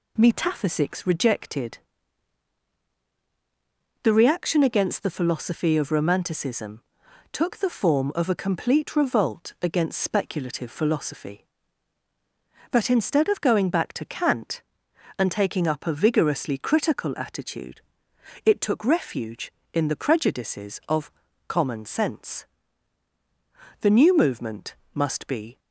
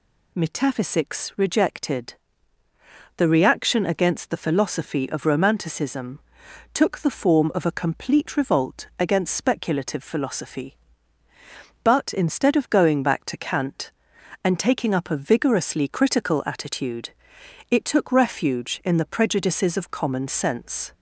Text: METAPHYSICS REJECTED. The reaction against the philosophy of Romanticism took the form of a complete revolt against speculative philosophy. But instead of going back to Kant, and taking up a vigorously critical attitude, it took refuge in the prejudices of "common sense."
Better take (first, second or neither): second